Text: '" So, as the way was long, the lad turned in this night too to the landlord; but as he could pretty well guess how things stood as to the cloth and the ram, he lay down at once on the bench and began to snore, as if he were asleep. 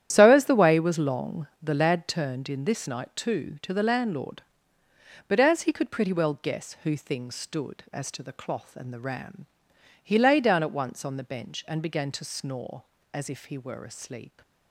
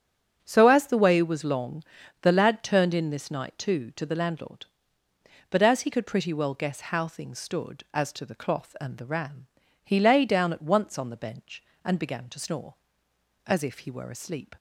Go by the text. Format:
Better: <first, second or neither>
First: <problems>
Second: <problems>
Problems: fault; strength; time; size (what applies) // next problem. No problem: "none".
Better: second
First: starts louder than the rest; strong; until 1.1 s; 10.5 dB // says "who" for "how"; at 6.8 s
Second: starts louder than the rest; strong; until 1.4 s; 7 dB